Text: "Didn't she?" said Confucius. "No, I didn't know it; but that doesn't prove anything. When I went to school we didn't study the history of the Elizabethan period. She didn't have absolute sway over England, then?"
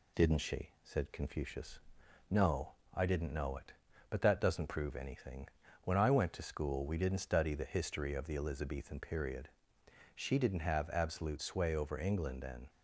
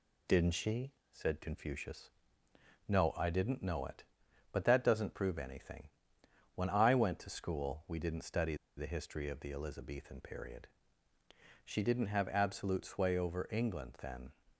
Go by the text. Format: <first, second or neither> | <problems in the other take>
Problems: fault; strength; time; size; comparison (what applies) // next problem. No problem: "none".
first | pauses between "study" and "the"; slight; at 8.5 s; 0.20 s long